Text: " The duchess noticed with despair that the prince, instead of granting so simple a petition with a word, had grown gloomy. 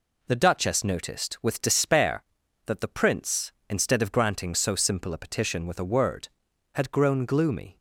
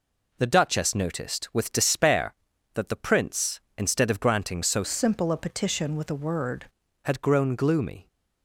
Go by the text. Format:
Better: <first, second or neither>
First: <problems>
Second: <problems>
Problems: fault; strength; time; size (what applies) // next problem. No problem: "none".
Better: first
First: none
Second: changes voice from "simple" to "word"; from 4.8 to 6.6 s; 1.8 s long